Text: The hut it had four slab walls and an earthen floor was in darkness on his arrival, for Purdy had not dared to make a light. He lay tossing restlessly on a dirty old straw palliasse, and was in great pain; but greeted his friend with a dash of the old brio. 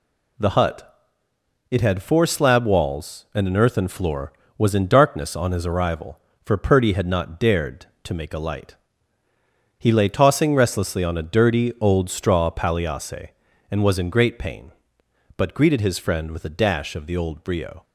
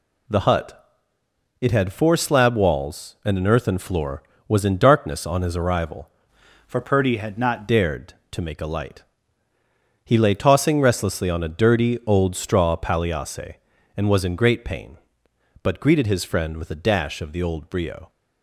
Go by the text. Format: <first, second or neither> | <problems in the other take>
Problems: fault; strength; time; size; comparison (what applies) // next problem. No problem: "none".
first | pauses between "hut" and "it"; noticeable; at 0.8 s; 0.78 s long; noticeable in the first // changes voice from "for" to "not"; from 6.6 to 7.6 s; 1.0 s long